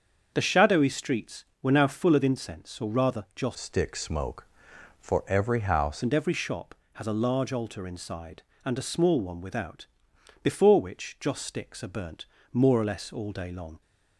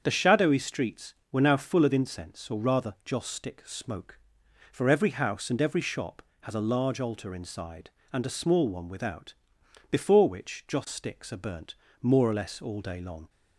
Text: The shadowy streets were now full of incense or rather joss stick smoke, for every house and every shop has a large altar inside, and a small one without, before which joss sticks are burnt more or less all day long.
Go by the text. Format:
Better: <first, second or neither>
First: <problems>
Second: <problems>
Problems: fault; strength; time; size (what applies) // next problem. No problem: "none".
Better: second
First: starts louder than the rest; until 1.3 s; 7 dB // changes voice from "stick" to "house"; from 3.5 to 6.0 s; 2.5 s long // pauses between "burnt" and "more"; slight; at 12.2 s; 0.26 s long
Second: starts louder than the rest; strong; until 1.0 s; 7.5 dB // pauses between "burnt" and "more"; slight; at 11.7 s; 0.26 s long